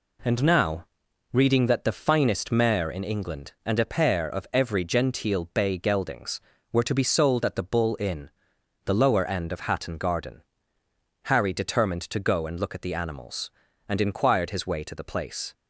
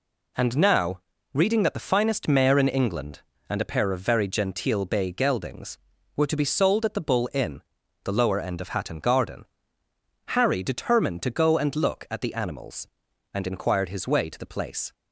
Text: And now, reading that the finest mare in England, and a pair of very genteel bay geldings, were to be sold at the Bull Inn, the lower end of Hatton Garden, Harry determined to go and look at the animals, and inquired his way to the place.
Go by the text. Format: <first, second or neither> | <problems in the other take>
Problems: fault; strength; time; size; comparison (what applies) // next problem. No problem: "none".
second | says "every" for "very"; at 4.5 s